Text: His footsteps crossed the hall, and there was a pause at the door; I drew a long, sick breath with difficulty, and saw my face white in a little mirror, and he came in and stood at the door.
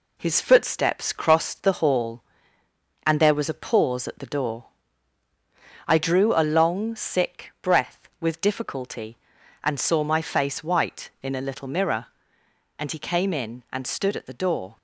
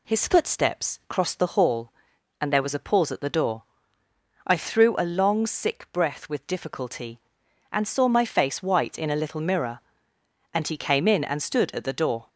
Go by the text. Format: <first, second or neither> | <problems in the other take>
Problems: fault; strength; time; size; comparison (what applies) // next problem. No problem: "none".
first | says "threw" for "drew"; at 4.5 s